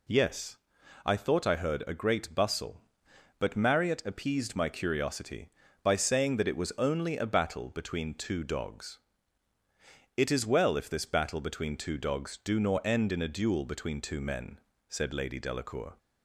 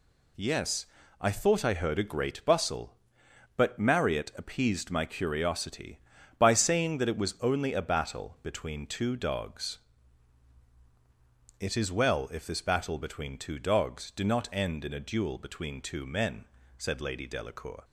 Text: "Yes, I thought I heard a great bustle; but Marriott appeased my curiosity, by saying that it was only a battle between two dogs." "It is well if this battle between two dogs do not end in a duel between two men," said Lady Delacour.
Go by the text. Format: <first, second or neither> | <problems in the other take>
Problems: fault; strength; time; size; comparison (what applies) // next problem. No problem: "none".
second | says "nor" for "not"; at 12.5 s